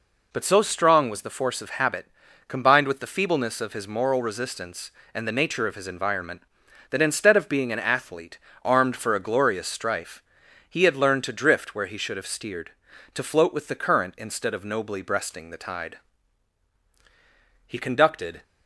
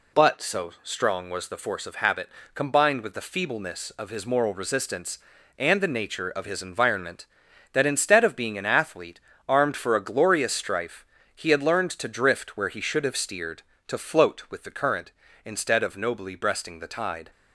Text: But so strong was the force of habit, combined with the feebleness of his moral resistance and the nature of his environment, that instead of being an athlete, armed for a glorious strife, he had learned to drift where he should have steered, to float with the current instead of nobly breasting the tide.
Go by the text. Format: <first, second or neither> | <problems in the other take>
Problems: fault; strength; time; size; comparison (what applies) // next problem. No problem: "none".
second | goes on to say "He conducted"; noticeable; from 17.6 s on; 0.76 s long